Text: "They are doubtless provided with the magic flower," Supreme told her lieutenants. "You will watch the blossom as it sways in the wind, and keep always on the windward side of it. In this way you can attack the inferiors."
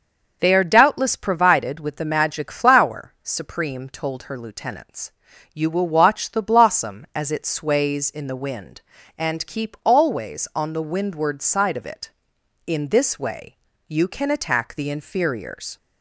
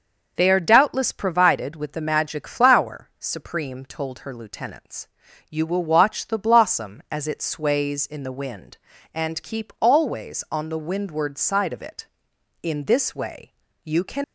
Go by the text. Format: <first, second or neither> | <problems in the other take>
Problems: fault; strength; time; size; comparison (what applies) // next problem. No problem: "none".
first | pauses between "way" and "you"; slight; at 13.5 s; 0.28 s long; slight in the first // stops before "attack the inferiors"; at 14.2 s